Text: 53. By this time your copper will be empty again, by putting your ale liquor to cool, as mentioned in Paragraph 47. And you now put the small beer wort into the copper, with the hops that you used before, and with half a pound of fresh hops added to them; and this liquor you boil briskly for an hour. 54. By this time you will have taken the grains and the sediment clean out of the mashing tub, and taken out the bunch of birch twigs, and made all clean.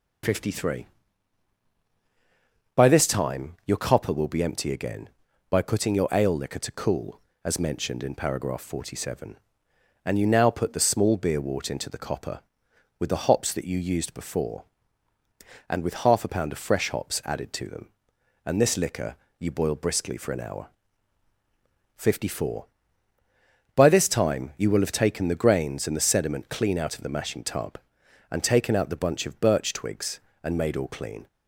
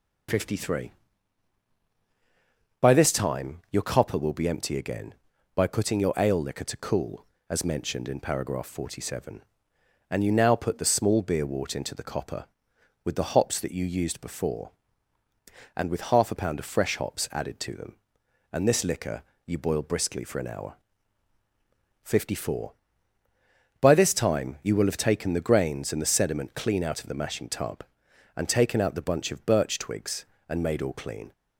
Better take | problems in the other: neither | pauses between "liquor" and "you"; slight; the same in both

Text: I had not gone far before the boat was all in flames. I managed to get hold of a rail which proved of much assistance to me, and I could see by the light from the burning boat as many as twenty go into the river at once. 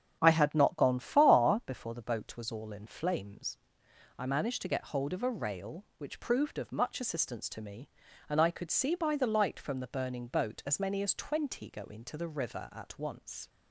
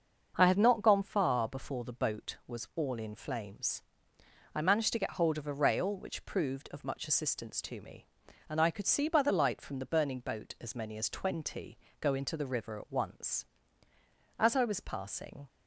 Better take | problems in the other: first | starts louder than the rest; until 1.3 s; 6.5 dB; strong in the first // pauses between "twenty" and "go"; slight; at 11.7 s; 0.24 s long // goes on to say "As I was passing"; noticeable; from 14.3 s on; 1.1 s long

